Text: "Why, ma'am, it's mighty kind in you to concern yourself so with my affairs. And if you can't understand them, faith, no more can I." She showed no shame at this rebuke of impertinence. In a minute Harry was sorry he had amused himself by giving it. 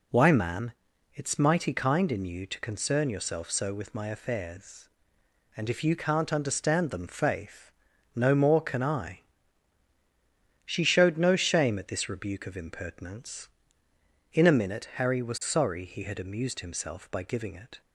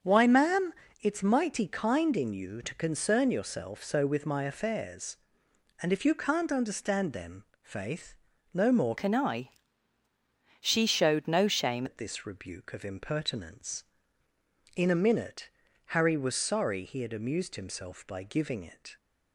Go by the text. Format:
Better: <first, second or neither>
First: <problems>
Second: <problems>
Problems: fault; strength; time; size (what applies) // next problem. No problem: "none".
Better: first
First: none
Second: starts louder than the rest; until 1.3 s; 7 dB // changes voice from "can" to "shame"; from 8.9 to 11.8 s; 2.9 s long // pauses between "minute" and "Harry"; at 15.4 s; 0.42 s long